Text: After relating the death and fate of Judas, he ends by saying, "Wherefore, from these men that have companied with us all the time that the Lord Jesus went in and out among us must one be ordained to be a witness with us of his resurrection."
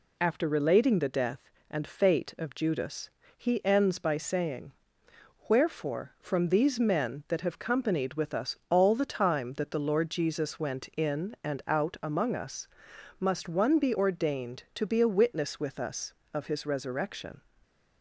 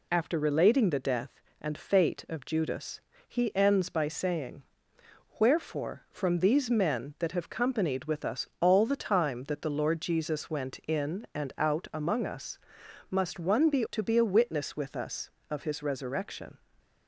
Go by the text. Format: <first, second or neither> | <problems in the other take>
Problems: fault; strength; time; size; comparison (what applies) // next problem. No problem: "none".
first | pauses between "us" and "must"; noticeable; at 12.5 s; 0.54 s long; noticeable in the first // skips "ordained"; at 13.8 s // stays silent after the last word; slight; from 16.5 s on; 0.5 s long